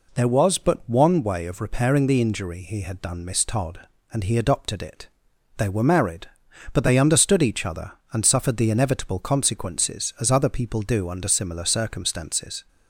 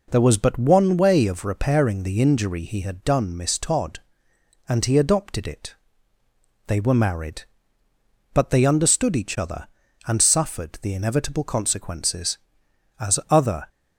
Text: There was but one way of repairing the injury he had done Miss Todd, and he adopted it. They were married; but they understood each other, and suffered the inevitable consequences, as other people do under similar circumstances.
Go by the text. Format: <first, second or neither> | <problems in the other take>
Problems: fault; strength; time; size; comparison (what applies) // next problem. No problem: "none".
first | stops before "people do under similar circumstances"; at 13.6 s